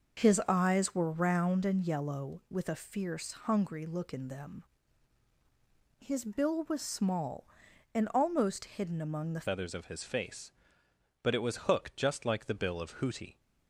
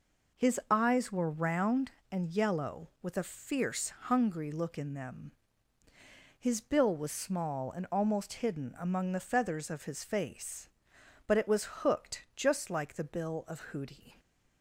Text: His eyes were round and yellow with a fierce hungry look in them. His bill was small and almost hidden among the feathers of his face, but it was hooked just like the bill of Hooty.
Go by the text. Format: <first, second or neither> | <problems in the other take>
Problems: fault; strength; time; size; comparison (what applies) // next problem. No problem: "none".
second | starts louder than the rest; noticeable; until 1.2 s; 6 dB // pauses between "fierce" and "hungry"; slight; at 3.2 s; 0.16 s long // changes voice at "feathers"; from 9.4 s on; 3.9 s long